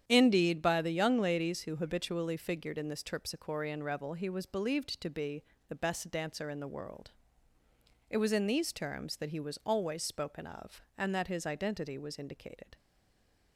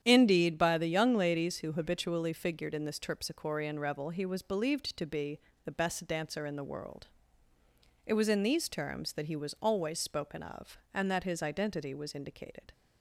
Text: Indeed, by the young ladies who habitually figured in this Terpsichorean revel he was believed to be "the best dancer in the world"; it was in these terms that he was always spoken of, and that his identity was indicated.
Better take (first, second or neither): second